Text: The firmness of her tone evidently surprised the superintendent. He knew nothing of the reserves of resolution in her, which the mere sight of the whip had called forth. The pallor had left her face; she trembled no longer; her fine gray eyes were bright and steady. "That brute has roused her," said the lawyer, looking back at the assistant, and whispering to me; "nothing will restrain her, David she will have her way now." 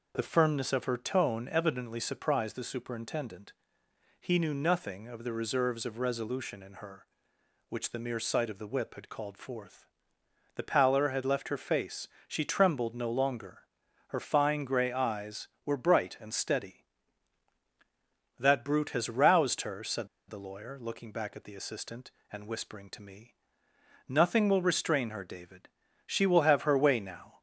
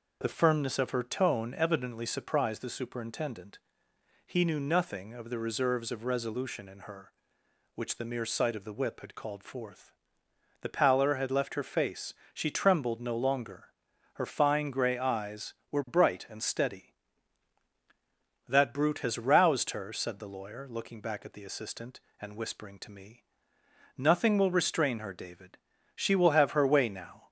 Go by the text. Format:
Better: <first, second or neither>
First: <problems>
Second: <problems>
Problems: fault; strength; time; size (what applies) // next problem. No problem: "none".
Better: second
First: pauses between "said" and "the"; slight; at 20.0 s; 0.20 s long // pauses between "David" and "she"; slight; at 25.6 s; 0.36 s long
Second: pauses between "David" and "she"; slight; at 25.5 s; 0.36 s long